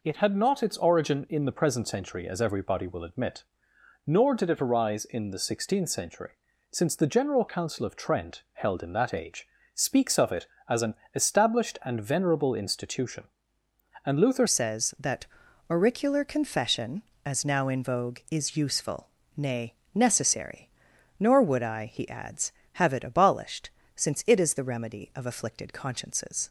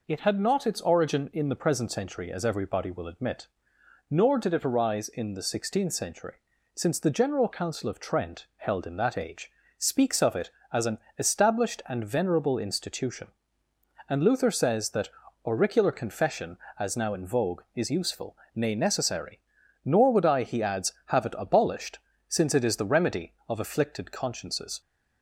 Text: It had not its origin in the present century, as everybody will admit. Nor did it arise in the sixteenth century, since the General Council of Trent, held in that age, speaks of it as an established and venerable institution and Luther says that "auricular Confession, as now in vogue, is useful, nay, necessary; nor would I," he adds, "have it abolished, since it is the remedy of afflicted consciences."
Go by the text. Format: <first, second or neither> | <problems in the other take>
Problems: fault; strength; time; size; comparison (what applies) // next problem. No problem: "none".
second | pauses between "an" and "established"; slight; at 10.9 s; 0.20 s long; slight in the second // changes voice at "says"; from 14.4 s on; 12.0 s long // pauses between "that" and "auricular"; at 15.2 s; 0.42 s long; also in the second